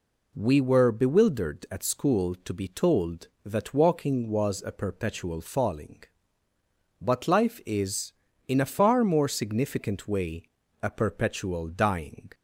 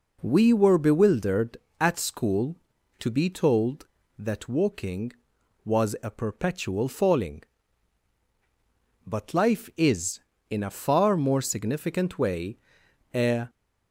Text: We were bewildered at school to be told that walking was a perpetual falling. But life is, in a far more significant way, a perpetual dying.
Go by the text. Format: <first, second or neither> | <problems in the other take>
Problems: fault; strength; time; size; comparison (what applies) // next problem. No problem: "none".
first | stops before "perpetual dying"; at 13.4 s